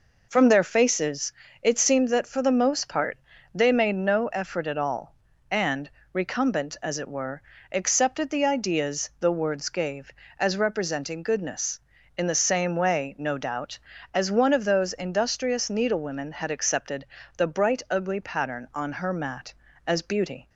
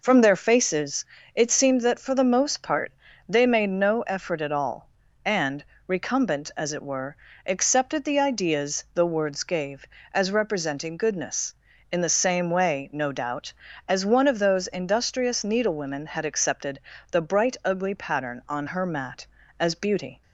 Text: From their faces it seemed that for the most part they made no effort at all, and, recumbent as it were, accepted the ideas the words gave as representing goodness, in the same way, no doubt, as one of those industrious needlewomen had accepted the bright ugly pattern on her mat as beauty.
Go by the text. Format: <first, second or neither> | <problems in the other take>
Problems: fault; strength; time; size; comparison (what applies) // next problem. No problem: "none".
neither | pauses between "faces" and "it"; slight; the same in both // pauses between "part" and "they"; the same in both // pauses between "accepted" and "the"; slight; the same in both